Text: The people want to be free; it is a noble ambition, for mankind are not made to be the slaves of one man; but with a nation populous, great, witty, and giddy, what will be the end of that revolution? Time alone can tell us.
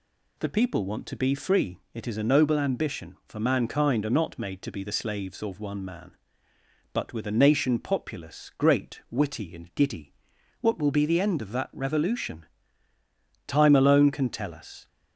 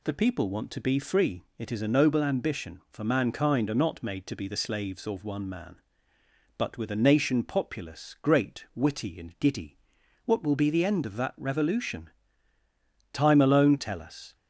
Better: first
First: none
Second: skips "can"; at 13.7 s

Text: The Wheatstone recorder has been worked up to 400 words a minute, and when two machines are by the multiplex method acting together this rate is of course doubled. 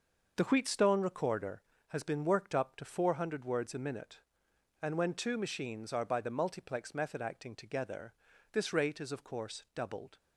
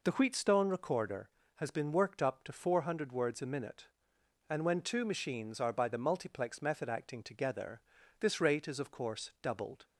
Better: second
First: gets quieter; strong; throughout; 8.5 dB // pauses between "together" and "this"; at 8.1 s; 0.38 s long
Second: pauses between "together" and "this"; at 7.8 s; 0.38 s long

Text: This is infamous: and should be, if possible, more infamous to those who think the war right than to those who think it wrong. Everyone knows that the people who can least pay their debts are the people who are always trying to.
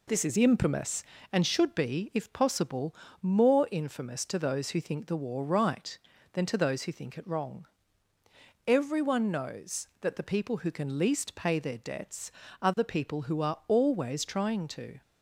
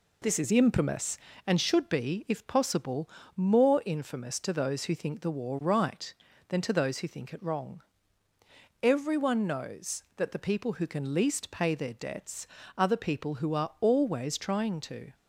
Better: neither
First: none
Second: none

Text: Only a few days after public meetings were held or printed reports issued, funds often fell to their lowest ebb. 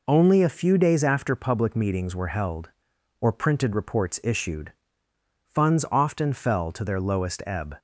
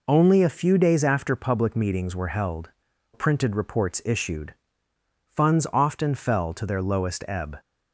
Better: first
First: none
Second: skips "or"; at 2.9 s

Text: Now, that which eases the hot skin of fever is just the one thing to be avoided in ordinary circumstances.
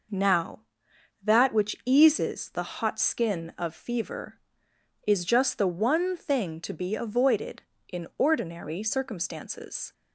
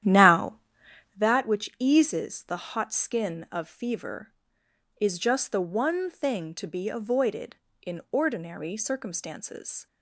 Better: first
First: none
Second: starts louder than the rest; strong; until 1.2 s; 11 dB

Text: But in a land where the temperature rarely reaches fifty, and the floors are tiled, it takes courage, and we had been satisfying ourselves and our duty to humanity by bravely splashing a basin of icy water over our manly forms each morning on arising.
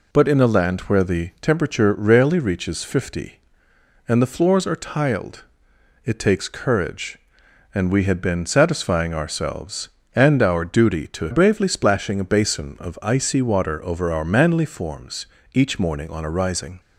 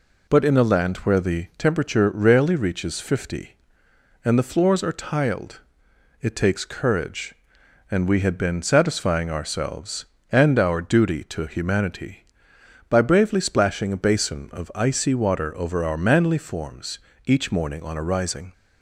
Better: second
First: skips "humanity by"; at 11.2 s // pauses between "forms" and "each"; slight; at 15.2 s; 0.26 s long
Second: pauses between "forms" and "each"; slight; at 16.9 s; 0.26 s long

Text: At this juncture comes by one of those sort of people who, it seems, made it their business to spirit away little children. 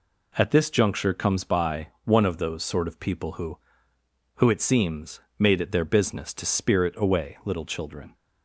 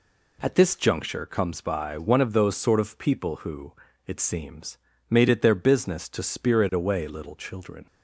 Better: second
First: pauses between "by" and "one"; slight; at 1.8 s; 0.18 s long // says "who" twice; at 4.3 s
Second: none

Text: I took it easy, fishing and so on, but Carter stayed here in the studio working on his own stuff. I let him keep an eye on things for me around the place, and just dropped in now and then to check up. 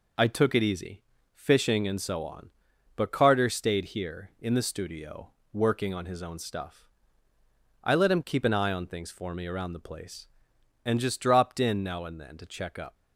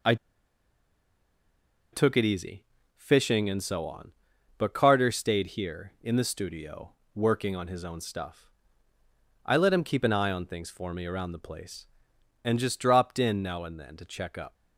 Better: first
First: pauses between "studio" and "working"; slight; at 5.2 s; 0.24 s long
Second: pauses between "I" and "took"; strong; at 0.1 s; 1.7 s long // pauses between "studio" and "working"; slight; at 6.9 s; 0.24 s long

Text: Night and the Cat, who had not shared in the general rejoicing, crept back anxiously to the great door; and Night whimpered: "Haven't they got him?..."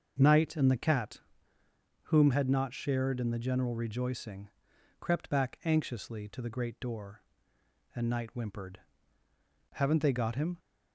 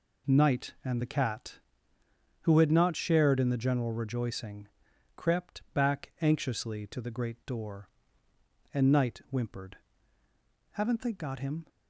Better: second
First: starts louder than the rest; until 1.2 s; 6.5 dB // says "whom" for "who"; at 2.0 s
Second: none

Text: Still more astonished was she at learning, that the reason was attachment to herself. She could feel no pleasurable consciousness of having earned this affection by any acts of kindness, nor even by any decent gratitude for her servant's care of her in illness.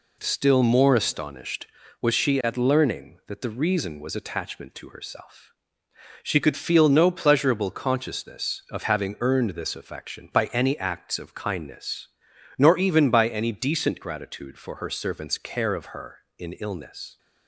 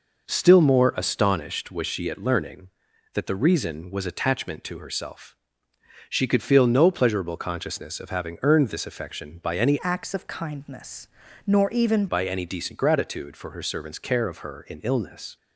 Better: first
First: none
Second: changes voice from "acts" to "even"; from 9.8 to 12.0 s; 2.2 s long

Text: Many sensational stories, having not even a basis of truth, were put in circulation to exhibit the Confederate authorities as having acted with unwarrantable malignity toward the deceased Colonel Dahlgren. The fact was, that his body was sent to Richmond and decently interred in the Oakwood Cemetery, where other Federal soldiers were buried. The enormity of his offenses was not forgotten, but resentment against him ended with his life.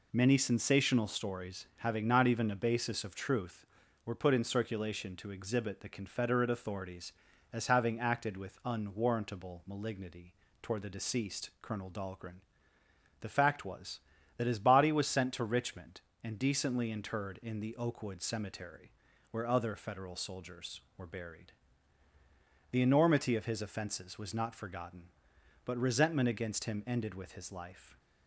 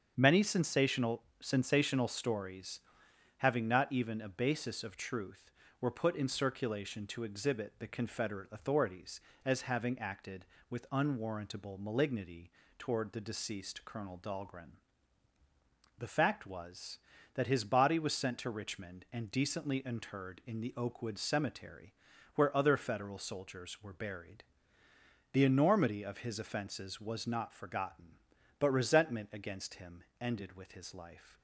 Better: first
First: pauses between "malignity" and "toward"; slight; at 10.3 s; 0.30 s long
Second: starts louder than the rest; strong; until 1.1 s; 7 dB // says "sensational" twice; at 1.4 s // pauses between "malignity" and "toward"; slight; at 12.5 s; 0.28 s long // pauses between "him" and "ended"; slight; at 30.0 s; 0.16 s long

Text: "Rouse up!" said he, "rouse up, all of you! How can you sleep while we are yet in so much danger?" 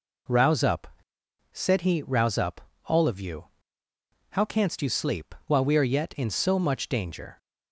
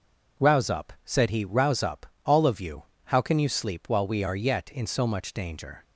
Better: second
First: says "canst" for "can"; at 4.4 s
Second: none

